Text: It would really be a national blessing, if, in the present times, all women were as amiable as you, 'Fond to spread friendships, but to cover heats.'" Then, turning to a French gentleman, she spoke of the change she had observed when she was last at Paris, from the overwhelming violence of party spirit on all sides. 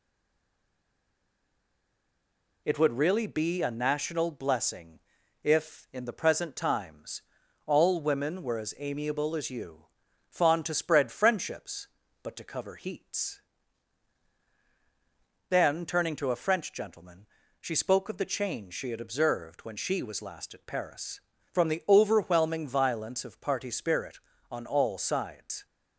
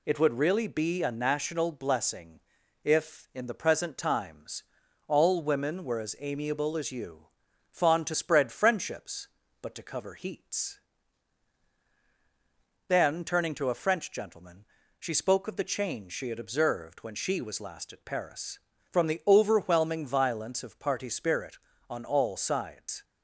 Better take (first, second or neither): second